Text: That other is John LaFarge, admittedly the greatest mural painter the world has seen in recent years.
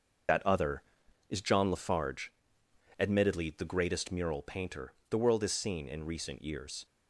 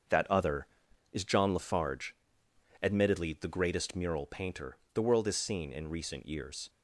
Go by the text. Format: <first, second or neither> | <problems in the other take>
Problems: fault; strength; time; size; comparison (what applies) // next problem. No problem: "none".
second | loses the start of "That"; at 0.2 s; 45 ms // starts louder than the rest; until 1.7 s; 6.5 dB; also in the second // pauses between "painter" and "the"; slight; at 4.9 s; 0.16 s long; slight in the second